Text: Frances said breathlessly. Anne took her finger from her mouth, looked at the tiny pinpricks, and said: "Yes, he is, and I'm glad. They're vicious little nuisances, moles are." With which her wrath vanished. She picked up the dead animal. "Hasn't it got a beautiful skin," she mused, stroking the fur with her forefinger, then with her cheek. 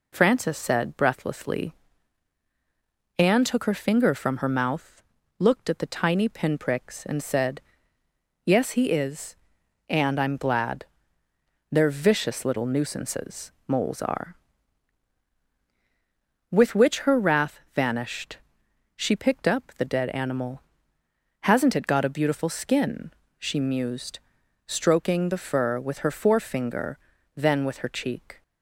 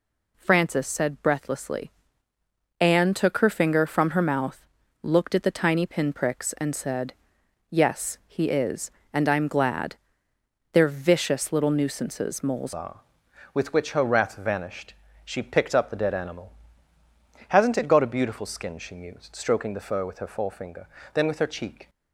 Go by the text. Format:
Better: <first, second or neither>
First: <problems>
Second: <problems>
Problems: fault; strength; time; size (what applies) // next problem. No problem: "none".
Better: first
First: none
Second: changes voice at "are"; from 12.7 s on; 9.1 s long